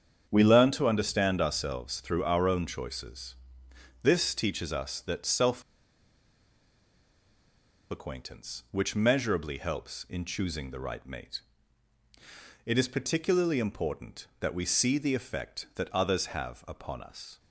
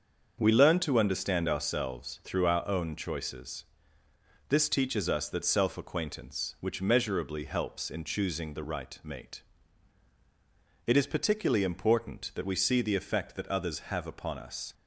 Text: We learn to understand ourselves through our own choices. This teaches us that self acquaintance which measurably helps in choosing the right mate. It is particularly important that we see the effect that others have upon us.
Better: second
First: starts louder than the rest; strong; until 1.3 s; 8 dB // pauses between "self" and "acquaintance"; strong; at 5.6 s; 2.2 s long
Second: starts louder than the rest; until 1.4 s; 6.5 dB

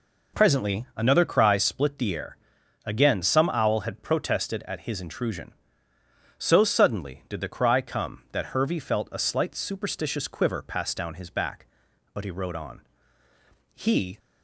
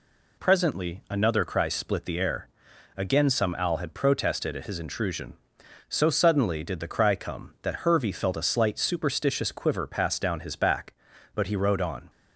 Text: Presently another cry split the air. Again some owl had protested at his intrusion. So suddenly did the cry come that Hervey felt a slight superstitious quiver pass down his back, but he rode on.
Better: second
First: goes on to say "He"; slight; from 13.7 s on; 0.44 s long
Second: none

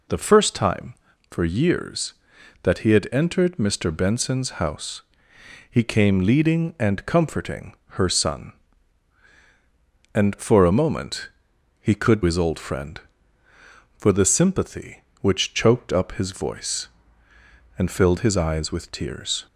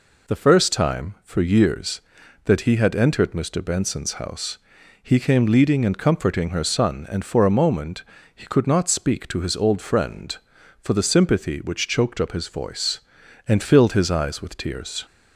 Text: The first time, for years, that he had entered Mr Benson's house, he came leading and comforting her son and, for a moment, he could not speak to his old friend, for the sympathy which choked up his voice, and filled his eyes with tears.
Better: second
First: pauses between "comforting" and "her"; slight; at 7.7 s; 0.24 s long // skips "not speak to"; at 12.2 s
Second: none

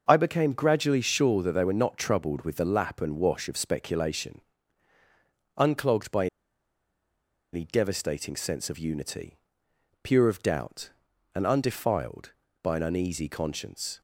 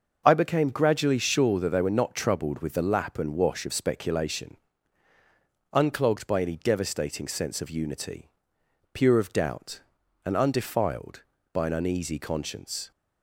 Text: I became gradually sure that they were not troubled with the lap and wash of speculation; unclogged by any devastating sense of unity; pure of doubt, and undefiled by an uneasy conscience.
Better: second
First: pauses between "by" and "any"; strong; at 6.2 s; 1.2 s long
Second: none

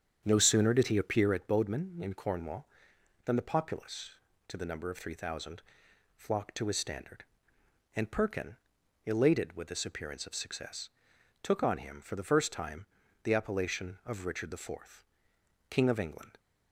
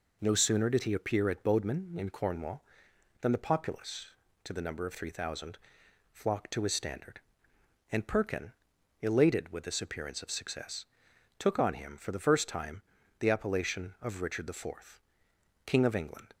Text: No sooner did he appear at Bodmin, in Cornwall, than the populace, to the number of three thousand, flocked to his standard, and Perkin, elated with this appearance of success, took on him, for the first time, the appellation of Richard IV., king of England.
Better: second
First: starts louder than the rest; strong; until 1.4 s; 8 dB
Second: none

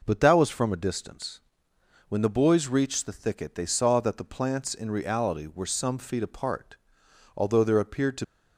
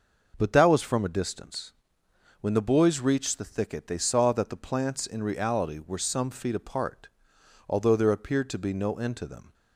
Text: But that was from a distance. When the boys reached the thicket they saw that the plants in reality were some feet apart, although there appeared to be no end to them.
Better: second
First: stops before "be no end to them"; at 8.2 s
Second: none

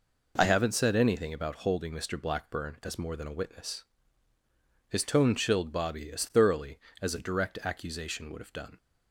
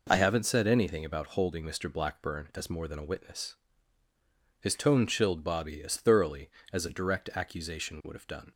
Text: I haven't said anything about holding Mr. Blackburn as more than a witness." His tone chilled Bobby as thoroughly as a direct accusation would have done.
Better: neither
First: none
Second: none

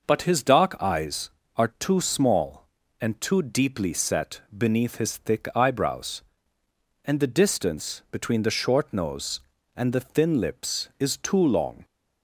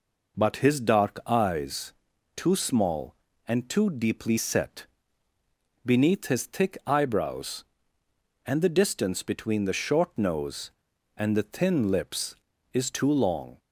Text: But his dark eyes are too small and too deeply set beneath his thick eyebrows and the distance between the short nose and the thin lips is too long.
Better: first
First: none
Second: skips "are"; at 2.1 s // pauses between "set" and "beneath"; noticeable; at 4.8 s; 0.98 s long

